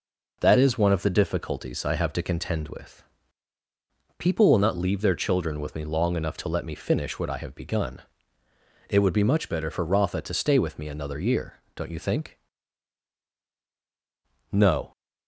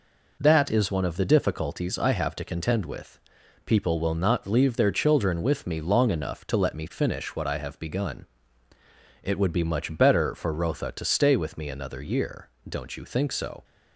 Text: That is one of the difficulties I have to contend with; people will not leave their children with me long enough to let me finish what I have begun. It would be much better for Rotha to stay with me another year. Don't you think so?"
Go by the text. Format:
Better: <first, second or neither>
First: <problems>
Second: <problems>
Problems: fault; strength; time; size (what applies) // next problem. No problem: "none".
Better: second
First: says "no" for "so"; at 14.5 s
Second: none